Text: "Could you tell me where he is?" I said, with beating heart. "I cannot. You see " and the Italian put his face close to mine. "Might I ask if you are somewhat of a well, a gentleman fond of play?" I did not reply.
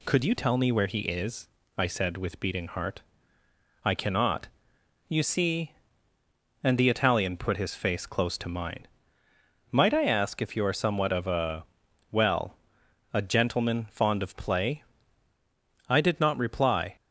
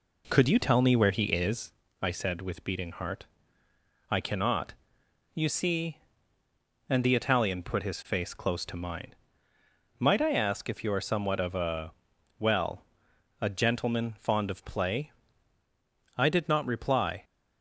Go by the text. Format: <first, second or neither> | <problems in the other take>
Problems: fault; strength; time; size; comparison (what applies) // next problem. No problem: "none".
first | starts louder than the rest; until 1.8 s; 4 dB // pauses between "a" and "well"; noticeable; at 11.9 s; 0.46 s long; noticeable in the first